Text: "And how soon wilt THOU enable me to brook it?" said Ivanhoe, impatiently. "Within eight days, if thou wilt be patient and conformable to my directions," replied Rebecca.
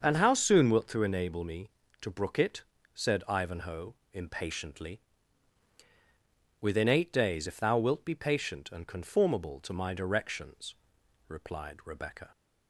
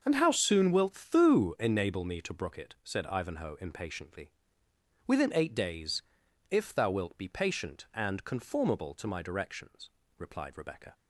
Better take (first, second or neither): neither